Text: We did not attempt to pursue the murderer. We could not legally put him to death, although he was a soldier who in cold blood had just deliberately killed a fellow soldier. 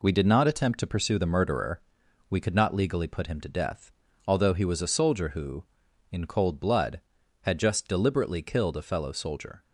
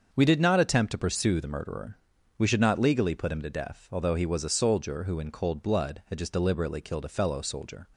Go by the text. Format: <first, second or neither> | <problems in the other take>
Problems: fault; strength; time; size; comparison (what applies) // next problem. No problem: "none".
first | starts louder than the rest; until 1.1 s; 6.5 dB // says "should" for "could"; at 2.4 s